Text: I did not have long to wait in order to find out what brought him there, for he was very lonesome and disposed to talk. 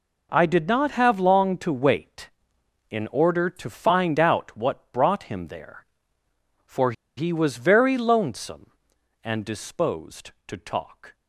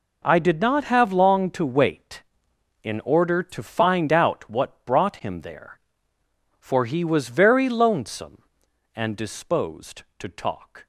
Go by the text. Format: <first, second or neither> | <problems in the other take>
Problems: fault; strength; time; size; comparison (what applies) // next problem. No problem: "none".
second | pauses between "for" and "he"; slight; at 6.9 s; 0.24 s long